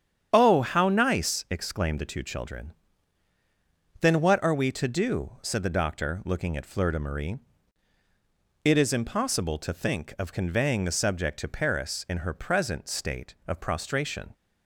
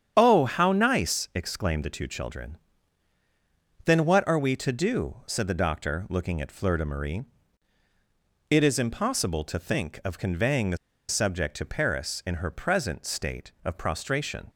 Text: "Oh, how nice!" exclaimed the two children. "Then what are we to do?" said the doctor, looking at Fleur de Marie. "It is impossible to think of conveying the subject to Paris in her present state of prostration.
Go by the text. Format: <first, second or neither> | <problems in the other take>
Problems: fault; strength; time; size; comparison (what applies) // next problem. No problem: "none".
first | starts louder than the rest; strong; until 1.1 s; 8.5 dB; strong in the first // pauses between "the" and "subject"; slight; at 10.7 s; 0.32 s long